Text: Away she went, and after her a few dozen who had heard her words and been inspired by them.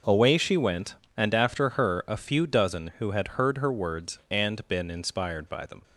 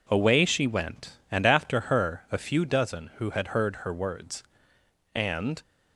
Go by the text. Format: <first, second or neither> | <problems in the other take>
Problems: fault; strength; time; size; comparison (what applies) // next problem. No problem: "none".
first | stops before "been inspired by them"; at 5.6 s